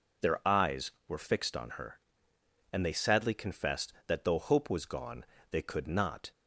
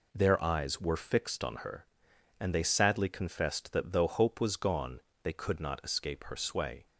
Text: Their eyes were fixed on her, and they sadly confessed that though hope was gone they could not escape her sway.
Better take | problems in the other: second | pauses between "gone" and "they"; slight; at 5.2 s; 0.26 s long; slight in the second // stops before "escape her sway"; at 6.3 s

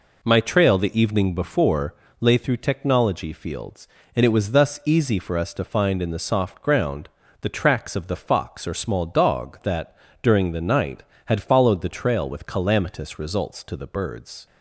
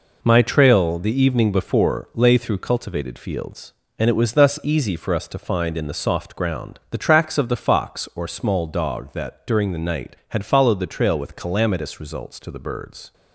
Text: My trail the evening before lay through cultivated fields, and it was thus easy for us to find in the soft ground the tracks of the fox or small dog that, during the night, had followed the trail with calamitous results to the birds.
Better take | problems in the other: second | pauses between "before" and "lay"; slight; at 1.9 s; 0.24 s long // says "technology" for "cultivated"; at 2.5 s // pauses between "ground" and "the"; slight; at 7.0 s; 0.30 s long

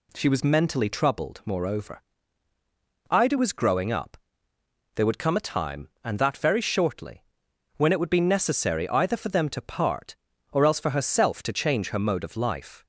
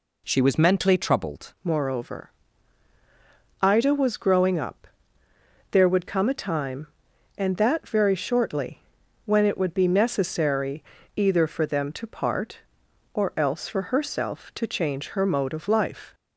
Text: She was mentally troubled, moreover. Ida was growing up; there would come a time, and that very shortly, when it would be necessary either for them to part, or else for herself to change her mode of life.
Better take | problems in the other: first | changes voice at "moreover"; from 1.6 s on; 14.5 s long // pauses between "necessary" and "either"; slight; at 10.8 s; 0.32 s long

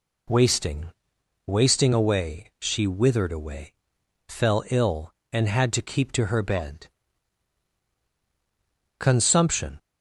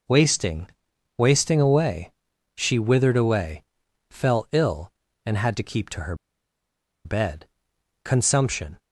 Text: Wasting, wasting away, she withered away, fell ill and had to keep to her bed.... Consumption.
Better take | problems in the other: first | pauses between "her" and "bed"; noticeable; at 6.1 s; 0.88 s long

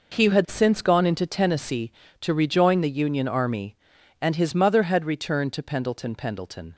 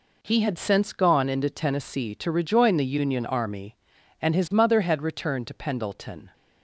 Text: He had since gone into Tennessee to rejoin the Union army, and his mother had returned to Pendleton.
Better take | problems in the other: second | says "Pendleton" twice; at 6.1 s

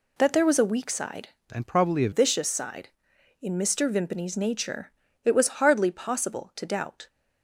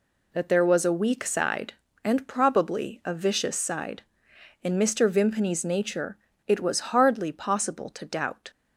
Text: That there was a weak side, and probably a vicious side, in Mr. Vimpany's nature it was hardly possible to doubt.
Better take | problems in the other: second | changes voice from "and" to "a"; from 1.5 to 2.0 s; 0.5 s long // pauses between "nature" and "it"; slight; at 4.9 s; 0.34 s long; slight in the second

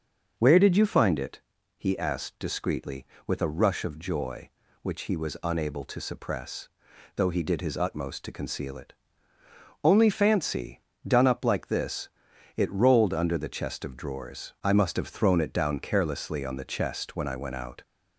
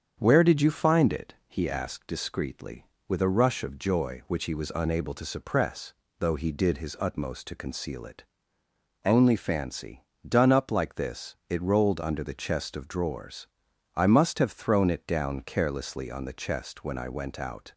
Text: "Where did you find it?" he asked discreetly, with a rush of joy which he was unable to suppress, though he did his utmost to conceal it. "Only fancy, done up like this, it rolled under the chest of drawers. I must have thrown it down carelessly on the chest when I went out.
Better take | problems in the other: neither | starts louder than the rest; the same in both

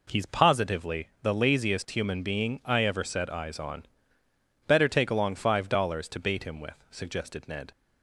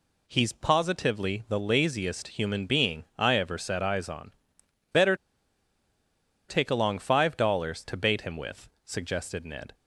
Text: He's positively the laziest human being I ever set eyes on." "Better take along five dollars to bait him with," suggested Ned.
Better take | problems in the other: first | pauses between "Better" and "take"; strong; at 5.1 s; 1.3 s long

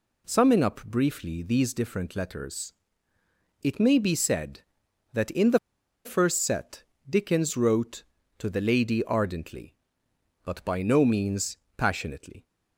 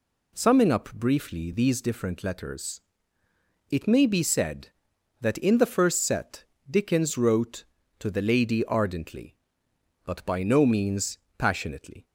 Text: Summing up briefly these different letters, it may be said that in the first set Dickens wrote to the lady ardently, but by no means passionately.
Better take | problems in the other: second | pauses between "the" and "first"; noticeable; at 5.5 s; 0.46 s long // pauses between "set" and "Dickens"; slight; at 6.8 s; 0.24 s long; slight in the second // pauses between "means" and "passionately"; slight; at 11.5 s; 0.20 s long; slight in the second

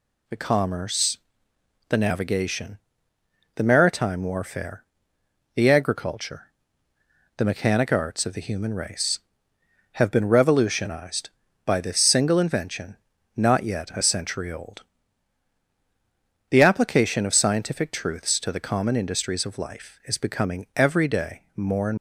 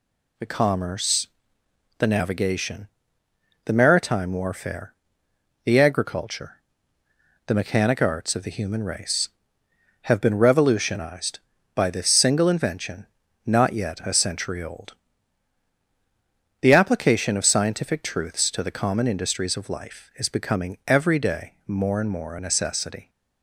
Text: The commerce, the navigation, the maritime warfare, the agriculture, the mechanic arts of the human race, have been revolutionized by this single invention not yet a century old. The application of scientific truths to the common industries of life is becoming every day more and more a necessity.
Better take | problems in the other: second | pauses between "invention" and "not"; at 12.9 s; 0.40 s long; also in the second // stops before "more a necessity"; at 21.9 s

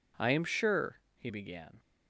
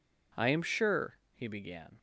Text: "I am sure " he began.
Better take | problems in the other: neither | none

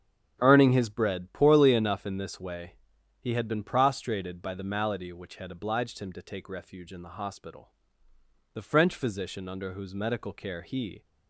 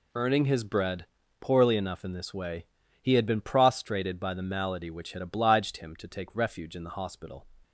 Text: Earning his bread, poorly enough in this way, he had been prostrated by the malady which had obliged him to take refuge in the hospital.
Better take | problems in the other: second | starts louder than the rest; strong; until 1.4 s; 8.5 dB // goes on to say "The French physician under whose medical care he"; strong; from 8.5 s on; 2.5 s long

